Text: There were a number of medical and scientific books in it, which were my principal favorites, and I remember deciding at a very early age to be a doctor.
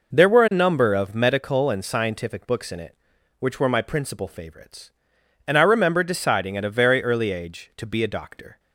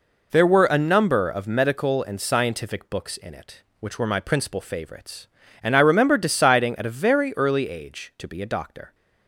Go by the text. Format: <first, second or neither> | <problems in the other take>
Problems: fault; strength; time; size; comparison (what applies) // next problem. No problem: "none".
neither | none